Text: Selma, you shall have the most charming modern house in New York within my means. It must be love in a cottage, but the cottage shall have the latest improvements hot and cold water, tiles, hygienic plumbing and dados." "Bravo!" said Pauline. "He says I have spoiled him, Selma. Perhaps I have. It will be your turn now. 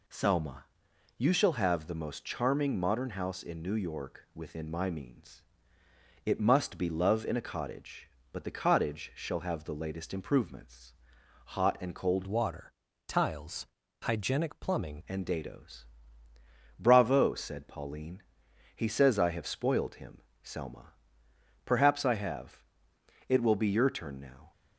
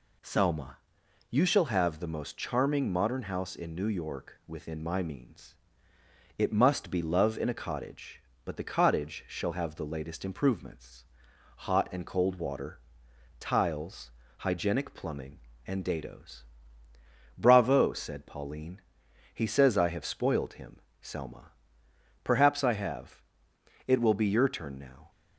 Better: second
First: pauses between "improvements" and "hot"; noticeable; at 10.9 s; 0.58 s long // changes voice from "water" to "plumbing"; from 12.2 to 15.0 s; 2.8 s long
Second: pauses between "improvements" and "hot"; noticeable; at 11.0 s; 0.58 s long

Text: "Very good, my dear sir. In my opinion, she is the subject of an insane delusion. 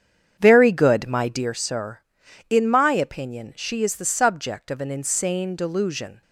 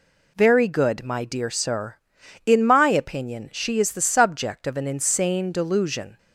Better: second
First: starts louder than the rest; strong; until 1.6 s; 8 dB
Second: none

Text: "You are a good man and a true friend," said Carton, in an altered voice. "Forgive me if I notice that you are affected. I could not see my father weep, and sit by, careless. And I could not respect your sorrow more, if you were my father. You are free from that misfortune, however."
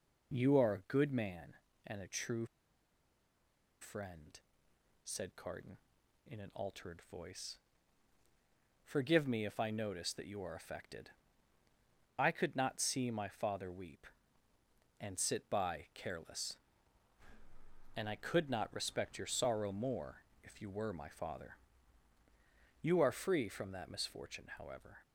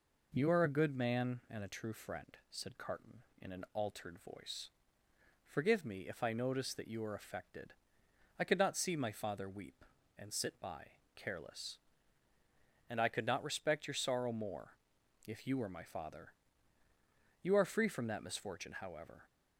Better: second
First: pauses between "true" and "friend"; strong; at 2.4 s; 1.3 s long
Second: none

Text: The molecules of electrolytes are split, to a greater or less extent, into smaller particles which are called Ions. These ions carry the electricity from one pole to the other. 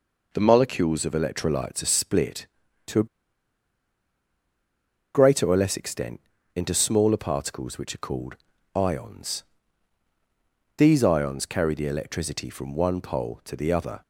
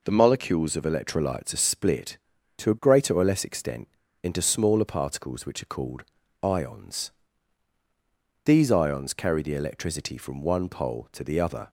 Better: second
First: pauses between "a" and "greater"; strong; at 3.0 s; 2.0 s long // pauses between "called" and "Ions"; at 8.3 s; 0.40 s long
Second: pauses between "called" and "Ions"; at 6.0 s; 0.40 s long

